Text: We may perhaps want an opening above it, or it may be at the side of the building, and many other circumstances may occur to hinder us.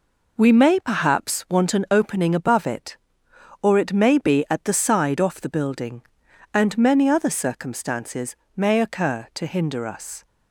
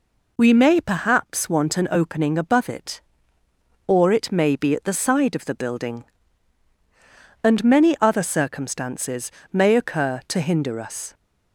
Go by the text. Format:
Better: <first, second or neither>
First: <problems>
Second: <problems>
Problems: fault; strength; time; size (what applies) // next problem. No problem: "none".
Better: second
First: says "off" for "of"; at 5.1 s // pauses between "circumstances" and "may"; slight; at 8.3 s; 0.18 s long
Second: pauses between "circumstances" and "may"; slight; at 9.2 s; 0.22 s long